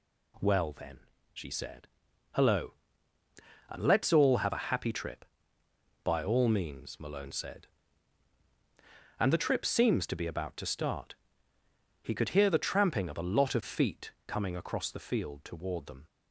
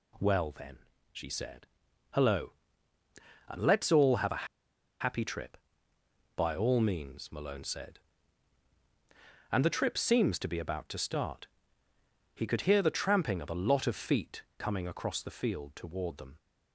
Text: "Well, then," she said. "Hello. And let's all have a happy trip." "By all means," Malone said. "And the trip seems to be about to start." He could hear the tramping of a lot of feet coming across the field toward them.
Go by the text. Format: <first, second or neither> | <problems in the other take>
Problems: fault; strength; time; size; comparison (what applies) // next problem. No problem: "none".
first | pauses between "a" and "happy"; noticeable; at 4.4 s; 0.54 s long